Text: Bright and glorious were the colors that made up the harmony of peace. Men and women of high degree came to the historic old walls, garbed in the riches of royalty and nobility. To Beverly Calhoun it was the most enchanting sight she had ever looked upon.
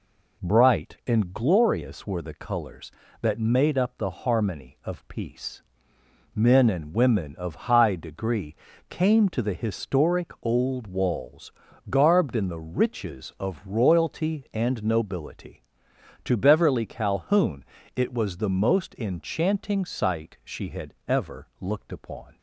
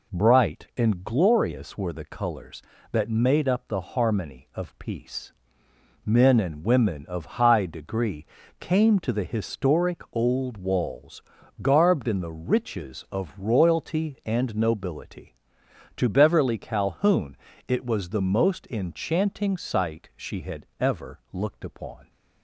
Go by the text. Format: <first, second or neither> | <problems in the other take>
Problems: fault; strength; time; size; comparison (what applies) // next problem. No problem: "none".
neither | pauses between "degree" and "came"; slight; the same in both // pauses between "Calhoun" and "it"; slight; the same in both